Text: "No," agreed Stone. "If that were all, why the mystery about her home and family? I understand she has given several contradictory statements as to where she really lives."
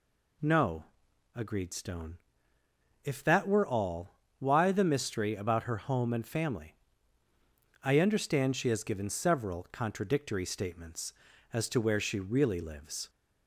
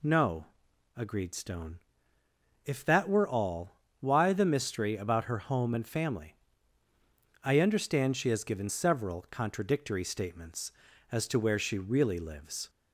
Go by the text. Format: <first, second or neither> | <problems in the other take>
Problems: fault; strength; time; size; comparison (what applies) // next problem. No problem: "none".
neither | none